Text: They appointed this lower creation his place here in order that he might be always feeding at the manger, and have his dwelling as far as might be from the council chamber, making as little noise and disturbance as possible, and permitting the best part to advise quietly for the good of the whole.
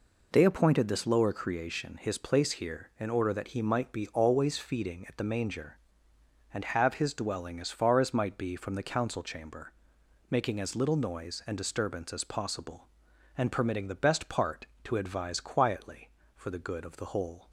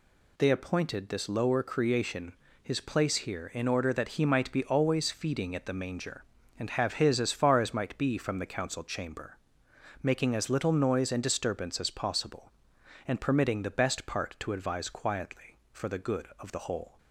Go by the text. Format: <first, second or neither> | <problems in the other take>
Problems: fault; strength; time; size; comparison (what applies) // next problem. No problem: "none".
first | pauses between "creation" and "his"; slight; at 2.3 s; 0.28 s long // skips "dwelling"; at 7.1 s